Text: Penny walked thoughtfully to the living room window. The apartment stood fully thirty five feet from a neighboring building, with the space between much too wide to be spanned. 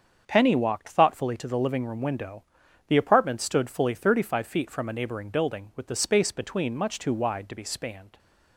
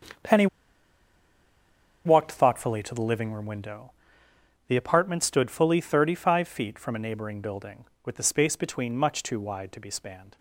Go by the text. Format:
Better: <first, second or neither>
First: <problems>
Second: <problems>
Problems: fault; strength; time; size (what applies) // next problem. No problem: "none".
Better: first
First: starts louder than the rest; strong; until 1.2 s; 7 dB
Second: starts louder than the rest; until 2.8 s; 7 dB // pauses between "Penny" and "walked"; strong; at 0.4 s; 1.5 s long